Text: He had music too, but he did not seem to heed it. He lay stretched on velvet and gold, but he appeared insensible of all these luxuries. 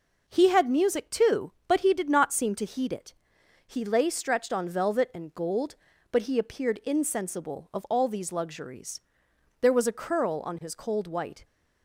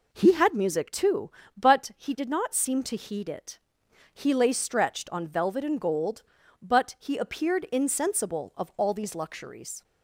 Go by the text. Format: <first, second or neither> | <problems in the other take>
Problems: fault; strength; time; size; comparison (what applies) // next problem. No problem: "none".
second | goes on to say "There was a curl on his cold white"; strong; from 9.6 s on; 1.8 s long